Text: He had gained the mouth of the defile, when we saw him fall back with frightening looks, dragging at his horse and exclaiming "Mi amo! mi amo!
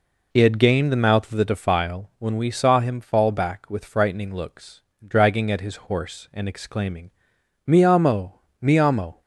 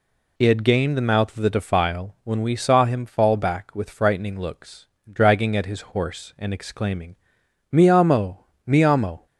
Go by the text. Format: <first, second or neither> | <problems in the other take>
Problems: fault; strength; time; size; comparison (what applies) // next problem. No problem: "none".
second | starts louder than the rest; until 1.4 s; 3.5 dB // pauses between "exclaiming" and "Mi"; noticeable; at 7.0 s; 0.56 s long; noticeable in the second